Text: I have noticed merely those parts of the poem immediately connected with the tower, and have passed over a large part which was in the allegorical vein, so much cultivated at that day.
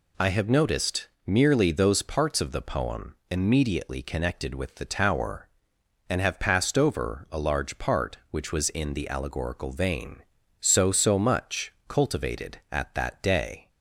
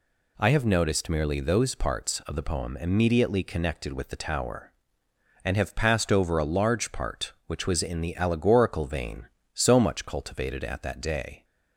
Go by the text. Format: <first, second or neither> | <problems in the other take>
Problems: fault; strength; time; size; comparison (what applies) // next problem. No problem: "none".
second | pauses between "noticed" and "merely"; slight; at 1.0 s; 0.18 s long // says "so" twice; at 10.8 s // pauses between "much" and "cultivated"; slight; at 11.7 s; 0.16 s long